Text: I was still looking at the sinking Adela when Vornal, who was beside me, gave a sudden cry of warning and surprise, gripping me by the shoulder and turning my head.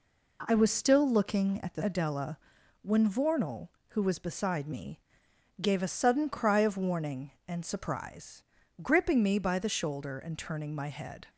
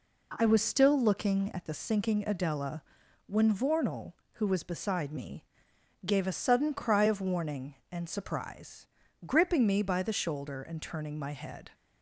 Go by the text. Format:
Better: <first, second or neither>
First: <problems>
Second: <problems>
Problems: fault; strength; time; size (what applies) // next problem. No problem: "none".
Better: second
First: skips "sinking"; at 1.8 s // pauses between "Adela" and "when"; at 2.3 s; 0.44 s long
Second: pauses between "Adela" and "when"; at 2.8 s; 0.44 s long